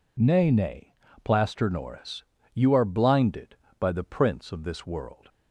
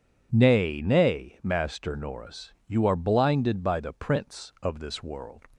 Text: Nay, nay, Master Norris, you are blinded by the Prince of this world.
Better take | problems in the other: second | says "Plaster" for "Master"; at 1.2 s

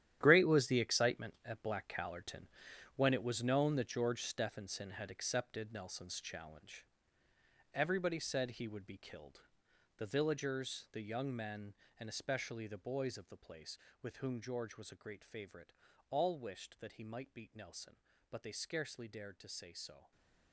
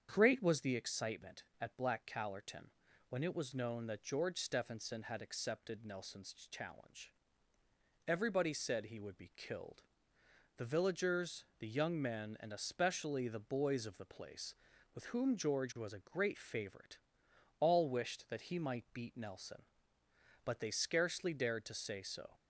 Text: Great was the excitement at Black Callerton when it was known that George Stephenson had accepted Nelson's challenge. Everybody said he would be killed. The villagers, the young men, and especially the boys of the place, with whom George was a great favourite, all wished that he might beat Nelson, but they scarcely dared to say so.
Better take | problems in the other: second | gets quieter; strong; throughout; 13 dB // starts louder than the rest; strong; until 1.2 s; 11 dB; strong in the second // pauses between "Callerton" and "when"; noticeable; at 2.4 s; 0.52 s long; also in the second // stays silent after the last word; slight; from 19.9 s on; 0.6 s long

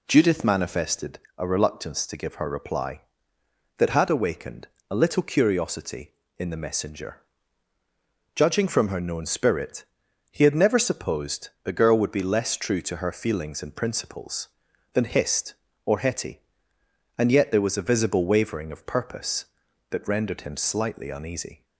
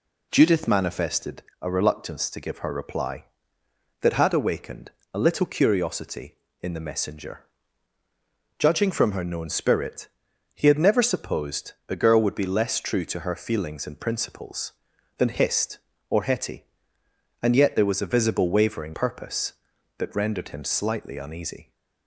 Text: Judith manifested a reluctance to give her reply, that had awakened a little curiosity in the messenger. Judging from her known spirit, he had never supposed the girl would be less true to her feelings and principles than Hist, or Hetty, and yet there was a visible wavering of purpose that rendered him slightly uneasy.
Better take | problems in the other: first | pauses between "manifested" and "a"; slight; at 1.4 s; 0.18 s long; slight in the first // pauses between "awakened" and "a"; slight; at 4.9 s; 0.24 s long; slight in the first // skips "of"; at 18.9 s

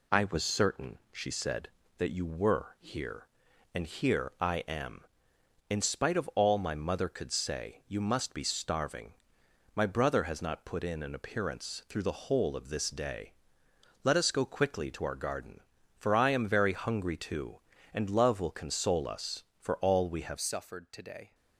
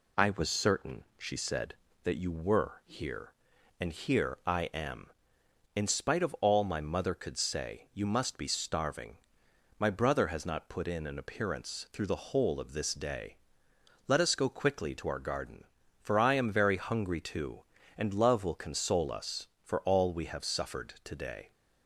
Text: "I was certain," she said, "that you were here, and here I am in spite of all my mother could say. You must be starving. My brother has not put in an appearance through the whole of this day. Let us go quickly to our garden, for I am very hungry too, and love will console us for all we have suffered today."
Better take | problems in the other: second | changes voice at "suffered"; from 20.4 s on; 0.9 s long

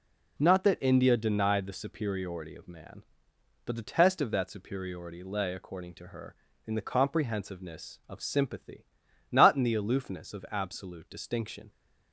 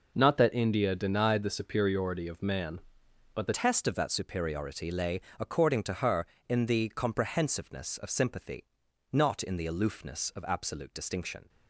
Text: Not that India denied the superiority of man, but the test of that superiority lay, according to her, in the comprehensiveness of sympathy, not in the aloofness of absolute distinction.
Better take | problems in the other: first | changes voice at "test"; from 3.5 s on; 7.9 s long

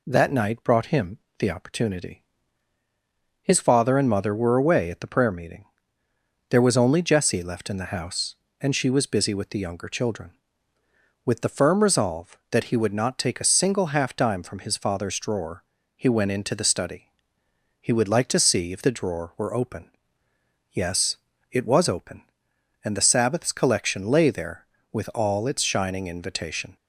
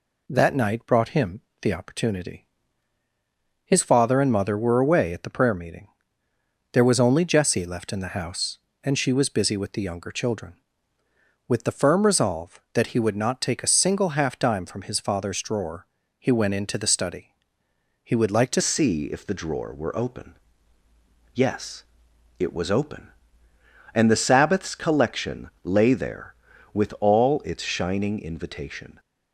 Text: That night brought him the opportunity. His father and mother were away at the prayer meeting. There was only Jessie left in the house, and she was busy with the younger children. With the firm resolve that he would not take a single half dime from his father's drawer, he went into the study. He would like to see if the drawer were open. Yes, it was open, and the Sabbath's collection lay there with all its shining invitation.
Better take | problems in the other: first | pauses between "him" and "the"; slight; at 1.4 s; 0.20 s long; slight in the first // changes voice at "see"; from 18.5 s on; 10.4 s long

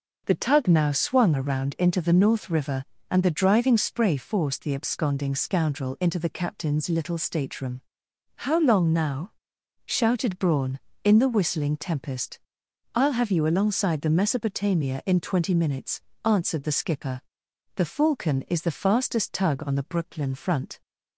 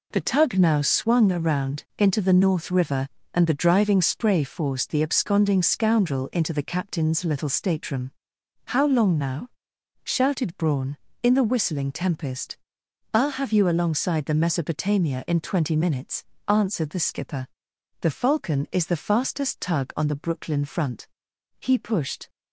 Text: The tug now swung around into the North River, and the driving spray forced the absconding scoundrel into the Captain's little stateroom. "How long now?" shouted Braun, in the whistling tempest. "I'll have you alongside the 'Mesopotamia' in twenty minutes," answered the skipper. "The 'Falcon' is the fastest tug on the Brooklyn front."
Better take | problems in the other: first | goes on to say "He pushed"; noticeable; from 21.5 s on; 0.70 s long

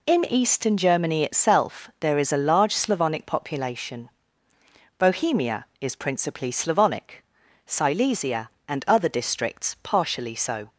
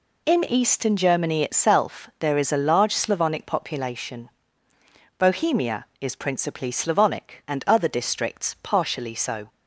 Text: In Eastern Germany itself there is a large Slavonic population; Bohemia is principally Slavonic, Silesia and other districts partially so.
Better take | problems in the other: first | skips "Silesia"; at 7.4 s

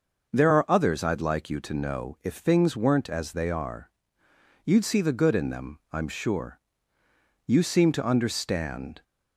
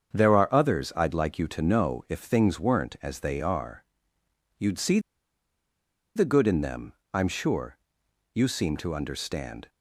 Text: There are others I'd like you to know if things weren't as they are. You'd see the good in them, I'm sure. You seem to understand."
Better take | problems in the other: first | starts louder than the rest; strong; until 1.2 s; 7.5 dB; noticeable in the first // pauses between "see" and "the"; at 4.9 s; 1.1 s long

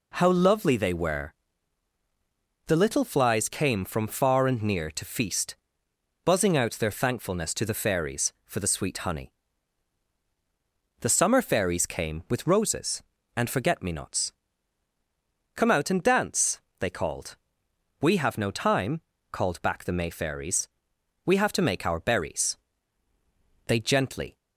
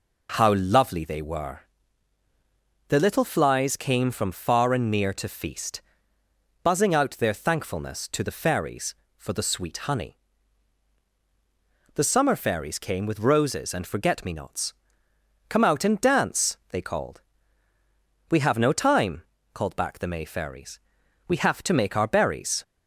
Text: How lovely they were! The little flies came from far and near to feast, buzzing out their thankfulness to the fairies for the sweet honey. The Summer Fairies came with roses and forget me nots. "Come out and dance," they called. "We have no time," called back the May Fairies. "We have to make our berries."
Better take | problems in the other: second | goes on to say "They gently"; noticeable; from 23.6 s on; 0.72 s long

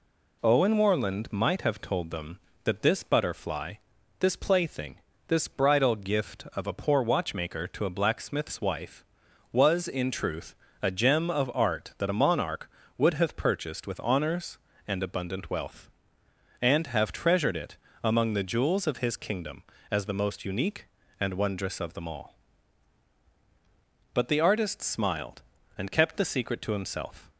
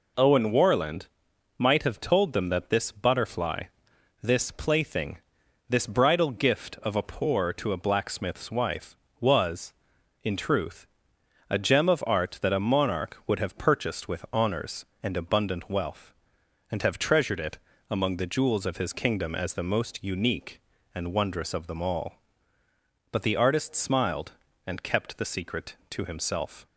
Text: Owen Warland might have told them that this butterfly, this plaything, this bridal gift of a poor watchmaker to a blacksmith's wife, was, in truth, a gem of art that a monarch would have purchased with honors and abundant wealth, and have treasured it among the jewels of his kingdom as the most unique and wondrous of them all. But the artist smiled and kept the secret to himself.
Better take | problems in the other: first | pauses between "Warland" and "might"; noticeable; at 1.0 s; 0.52 s long // skips "watchmaker"; at 7.5 s // pauses between "it" and "among"; slight; at 17.5 s; 0.32 s long; slight in the first

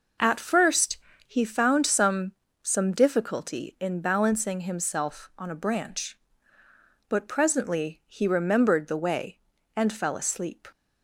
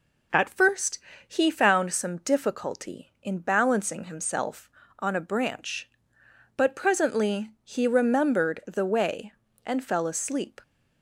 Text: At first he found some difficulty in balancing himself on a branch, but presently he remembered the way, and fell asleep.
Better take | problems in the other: second | pauses between "first" and "he"; slight; at 0.9 s; 0.30 s long; slight in the second // says "some" twice; at 2.6 s

